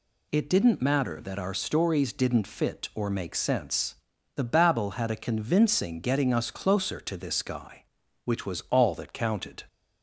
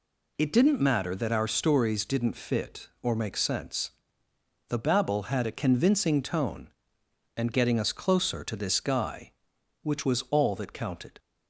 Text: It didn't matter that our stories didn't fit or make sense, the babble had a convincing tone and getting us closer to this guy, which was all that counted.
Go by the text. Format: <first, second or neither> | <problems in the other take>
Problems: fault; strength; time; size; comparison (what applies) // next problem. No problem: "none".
second | skips "tone and"; at 6.0 s